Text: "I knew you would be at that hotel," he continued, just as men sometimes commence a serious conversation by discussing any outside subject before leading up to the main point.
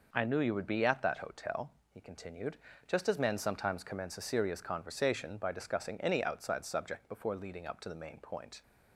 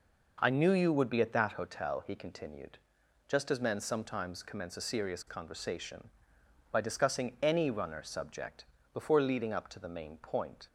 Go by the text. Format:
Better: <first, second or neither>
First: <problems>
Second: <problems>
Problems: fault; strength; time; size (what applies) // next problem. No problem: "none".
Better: first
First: none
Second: says "runner" for "outside"; at 7.7 s // pauses between "subject" and "before"; slight; at 8.6 s; 0.28 s long